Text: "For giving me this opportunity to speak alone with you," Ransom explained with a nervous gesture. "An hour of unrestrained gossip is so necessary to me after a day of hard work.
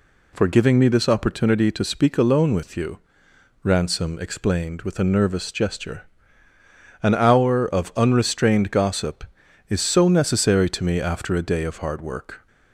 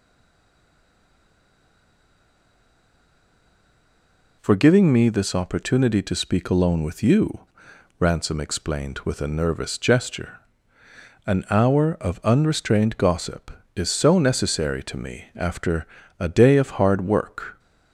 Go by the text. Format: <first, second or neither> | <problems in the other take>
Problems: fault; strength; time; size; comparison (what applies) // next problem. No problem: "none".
first | stays silent before the first word; strong; until 4.4 s; 4.4 s long // pauses between "after" and "a"; slight; at 15.8 s; 0.34 s long